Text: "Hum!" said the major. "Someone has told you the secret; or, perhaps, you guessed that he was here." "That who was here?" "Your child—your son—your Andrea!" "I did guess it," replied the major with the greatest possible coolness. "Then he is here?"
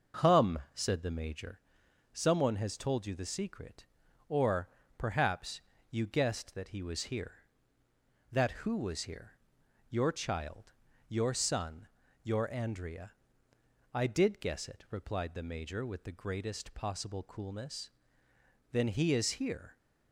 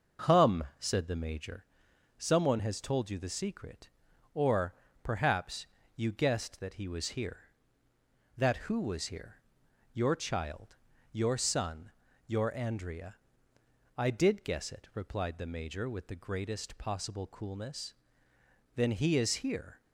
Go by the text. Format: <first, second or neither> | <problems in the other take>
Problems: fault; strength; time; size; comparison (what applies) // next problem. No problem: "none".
neither | none